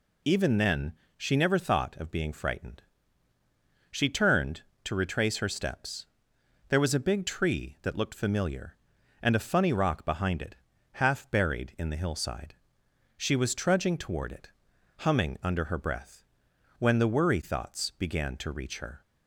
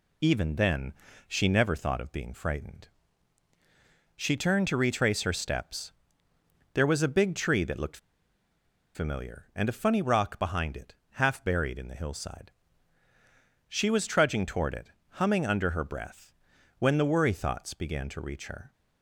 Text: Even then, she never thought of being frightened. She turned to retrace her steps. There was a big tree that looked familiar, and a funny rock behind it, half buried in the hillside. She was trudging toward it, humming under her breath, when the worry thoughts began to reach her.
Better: first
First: none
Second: pauses between "looked" and "familiar"; noticeable; at 7.9 s; 0.97 s long

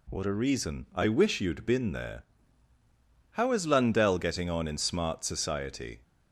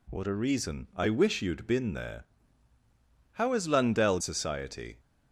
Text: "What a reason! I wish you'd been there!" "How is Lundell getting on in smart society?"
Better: first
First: none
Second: skips "getting on in smart"; at 4.2 s

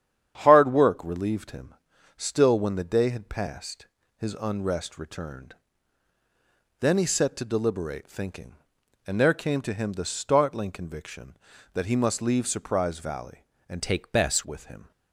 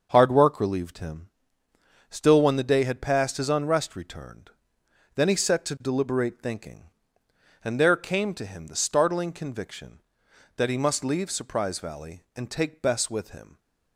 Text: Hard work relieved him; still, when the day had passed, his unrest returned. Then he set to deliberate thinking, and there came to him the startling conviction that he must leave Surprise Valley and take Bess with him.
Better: second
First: starts louder than the rest; strong; until 1.4 s; 9 dB // changes voice from "take" to "Bess"; from 13.8 to 14.4 s; 0.6 s long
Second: starts louder than the rest; until 1.1 s; 6 dB

